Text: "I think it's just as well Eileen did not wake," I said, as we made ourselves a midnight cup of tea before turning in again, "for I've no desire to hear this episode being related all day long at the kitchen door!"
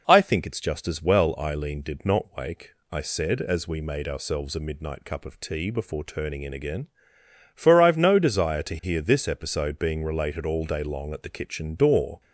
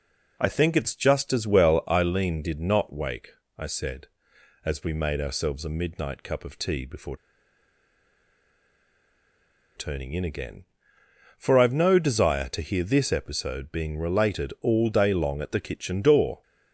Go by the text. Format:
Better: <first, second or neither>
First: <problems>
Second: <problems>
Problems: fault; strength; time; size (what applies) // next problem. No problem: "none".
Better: first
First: none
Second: pauses between "before" and "turning"; strong; at 7.1 s; 2.5 s long